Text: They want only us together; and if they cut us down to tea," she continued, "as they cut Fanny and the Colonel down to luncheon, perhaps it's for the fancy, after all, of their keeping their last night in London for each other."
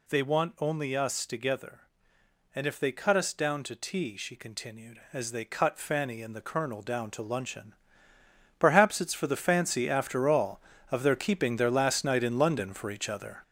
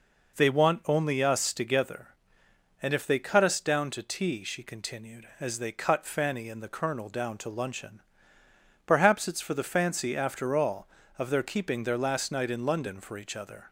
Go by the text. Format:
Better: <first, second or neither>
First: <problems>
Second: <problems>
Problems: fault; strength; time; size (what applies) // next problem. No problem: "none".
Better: second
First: gets louder; noticeable; throughout; 5.5 dB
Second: none